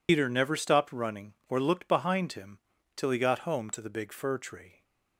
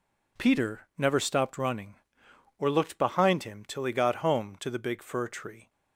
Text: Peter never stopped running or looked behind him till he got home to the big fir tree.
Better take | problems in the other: second | loses the start of "Peter"; at 0.0 s; 115 ms // pauses between "him" and "till"; slight; at 2.5 s; 0.36 s long

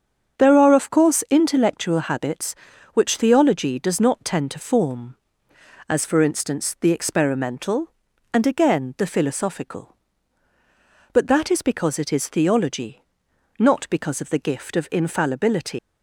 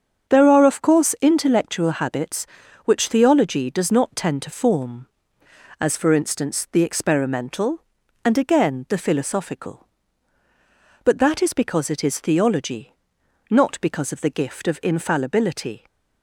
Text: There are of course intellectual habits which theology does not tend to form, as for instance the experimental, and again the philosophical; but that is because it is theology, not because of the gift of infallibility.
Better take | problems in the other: second | starts louder than the rest; strong; until 1.4 s; 7 dB; strong in the second // leaves "infallibility" unfinished; at 15.7 s; 165 ms

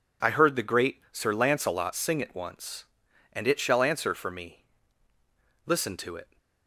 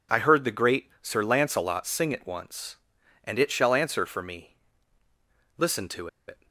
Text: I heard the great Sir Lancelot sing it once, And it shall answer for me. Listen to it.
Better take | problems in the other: first | pauses between "to" and "it"; slight; at 6.0 s; 0.21 s long

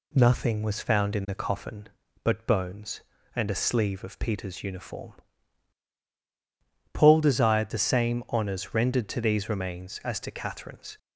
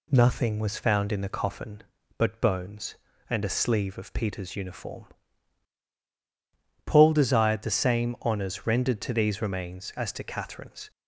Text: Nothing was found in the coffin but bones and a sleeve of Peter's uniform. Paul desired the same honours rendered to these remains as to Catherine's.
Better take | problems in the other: neither | none

